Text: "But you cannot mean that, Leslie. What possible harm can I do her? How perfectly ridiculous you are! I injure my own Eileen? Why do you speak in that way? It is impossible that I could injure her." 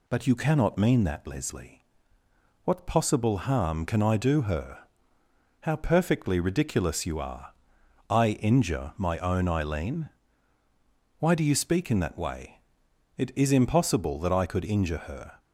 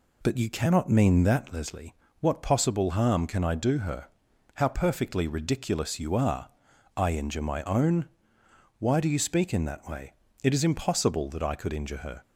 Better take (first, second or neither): first